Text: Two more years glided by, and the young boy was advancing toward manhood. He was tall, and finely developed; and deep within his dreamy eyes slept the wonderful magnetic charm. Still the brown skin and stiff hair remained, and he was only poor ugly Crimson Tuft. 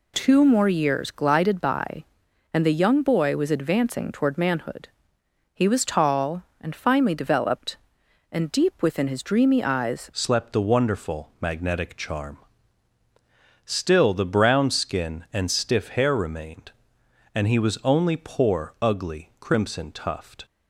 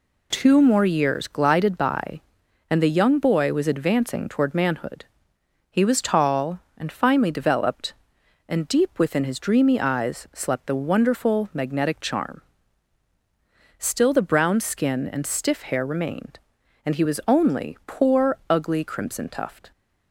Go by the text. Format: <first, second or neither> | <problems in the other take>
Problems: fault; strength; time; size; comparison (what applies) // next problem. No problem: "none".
second | changes voice at "slept"; from 10.1 s on; 10.3 s long